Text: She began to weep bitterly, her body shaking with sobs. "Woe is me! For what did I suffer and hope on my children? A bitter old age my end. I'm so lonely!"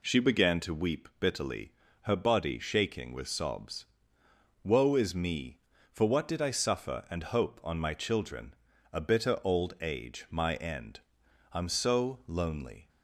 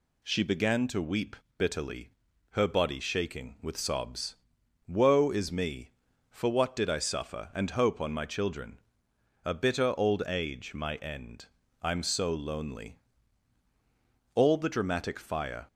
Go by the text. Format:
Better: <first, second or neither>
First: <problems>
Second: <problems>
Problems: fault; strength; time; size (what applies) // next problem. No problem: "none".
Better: first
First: none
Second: pauses between "weep" and "bitterly"; slight; at 1.3 s; 0.22 s long // goes on to say "All the dramatic fire"; from 14.3 s on; 1.3 s long